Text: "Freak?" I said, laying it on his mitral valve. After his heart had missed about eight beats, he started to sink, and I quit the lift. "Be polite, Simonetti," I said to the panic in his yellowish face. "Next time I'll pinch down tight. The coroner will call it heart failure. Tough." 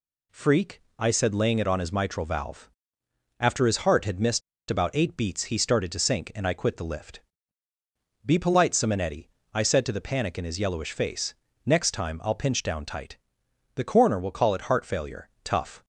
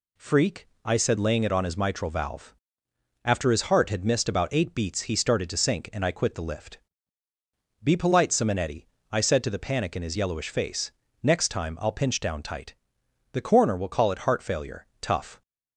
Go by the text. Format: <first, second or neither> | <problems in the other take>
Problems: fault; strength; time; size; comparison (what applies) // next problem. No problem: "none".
second | pauses between "missed" and "about"; slight; at 4.4 s; 0.29 s long